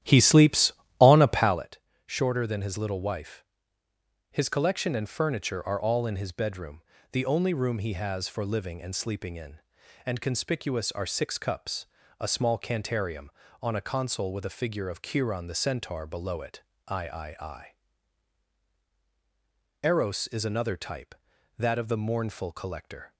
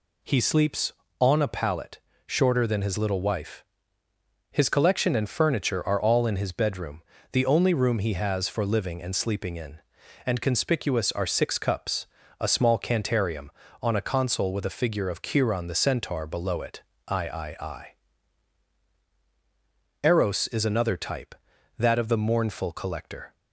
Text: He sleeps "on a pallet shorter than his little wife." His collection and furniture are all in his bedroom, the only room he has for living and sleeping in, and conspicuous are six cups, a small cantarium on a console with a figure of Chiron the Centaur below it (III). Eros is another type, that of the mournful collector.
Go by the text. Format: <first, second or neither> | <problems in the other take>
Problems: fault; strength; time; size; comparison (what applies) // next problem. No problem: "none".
second | starts louder than the rest; strong; until 1.7 s; 12 dB // pauses between "pallet" and "shorter"; slight; at 1.7 s; 0.28 s long; slight in the second